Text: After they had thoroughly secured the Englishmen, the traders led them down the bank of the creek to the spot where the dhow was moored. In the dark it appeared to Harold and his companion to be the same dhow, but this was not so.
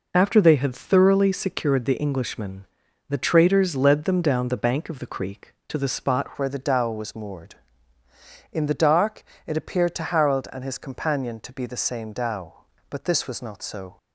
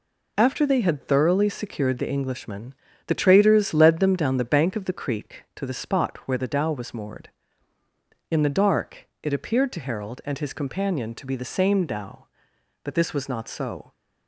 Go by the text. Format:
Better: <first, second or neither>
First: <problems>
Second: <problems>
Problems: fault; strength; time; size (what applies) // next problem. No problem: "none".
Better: second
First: changes voice at "where"; from 6.3 s on; 7.6 s long // pauses between "dark" and "it"; slight; at 9.2 s; 0.24 s long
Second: none